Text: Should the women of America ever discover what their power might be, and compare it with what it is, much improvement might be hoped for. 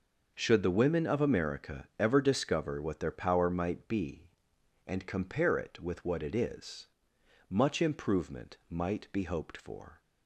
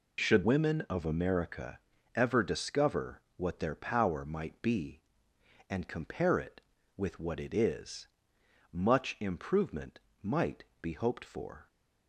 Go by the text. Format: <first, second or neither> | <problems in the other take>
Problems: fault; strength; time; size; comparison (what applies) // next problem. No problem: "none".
first | skips "the"; at 0.4 s // pauses between "America" and "ever"; at 1.7 s; 0.38 s long // pauses between "discover" and "what"; slight; at 3.1 s; 0.16 s long // pauses between "improvement" and "might"; slight; at 9.9 s; 0.24 s long // pauses between "might" and "be"; slight; at 10.6 s; 0.18 s long